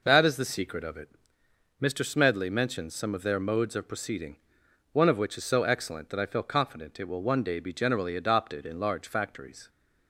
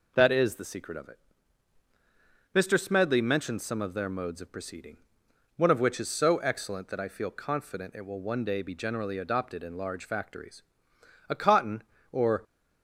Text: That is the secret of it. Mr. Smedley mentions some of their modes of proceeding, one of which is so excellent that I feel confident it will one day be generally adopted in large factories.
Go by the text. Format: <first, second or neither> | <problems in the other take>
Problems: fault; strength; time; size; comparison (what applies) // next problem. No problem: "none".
first | goes on to say "A cotton or"; noticeable; from 11.2 s on; 1.1 s long